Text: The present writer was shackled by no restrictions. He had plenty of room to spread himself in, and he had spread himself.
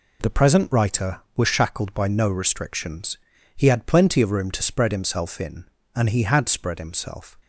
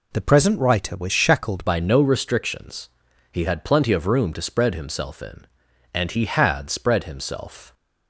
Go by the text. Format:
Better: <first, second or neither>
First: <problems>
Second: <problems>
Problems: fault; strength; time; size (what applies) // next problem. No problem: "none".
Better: first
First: none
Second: changes voice at "by"; from 1.6 s on; 6.1 s long